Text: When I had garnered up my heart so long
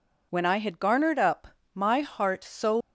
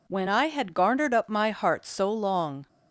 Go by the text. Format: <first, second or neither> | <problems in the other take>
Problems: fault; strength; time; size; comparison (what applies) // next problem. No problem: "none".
second | pauses between "up" and "my"; slight; at 1.4 s; 0.26 s long // stops before "long"; at 2.8 s